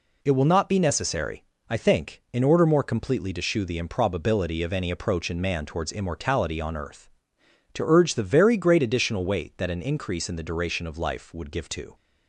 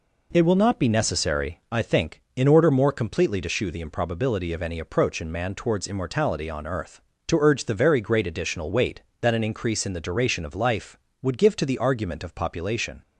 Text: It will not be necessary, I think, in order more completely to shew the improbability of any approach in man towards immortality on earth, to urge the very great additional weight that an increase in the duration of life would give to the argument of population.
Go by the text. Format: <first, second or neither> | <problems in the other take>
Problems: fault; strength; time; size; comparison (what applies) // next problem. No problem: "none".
second | stops before "the argument of population"; at 11.9 s